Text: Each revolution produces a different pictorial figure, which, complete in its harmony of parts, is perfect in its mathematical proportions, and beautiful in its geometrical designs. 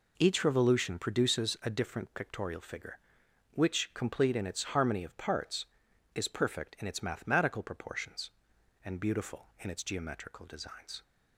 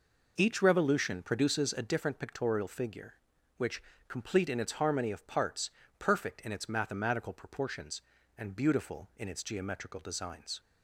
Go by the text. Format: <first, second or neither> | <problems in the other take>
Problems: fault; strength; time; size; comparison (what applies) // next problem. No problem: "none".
first | skips "is"; at 5.8 s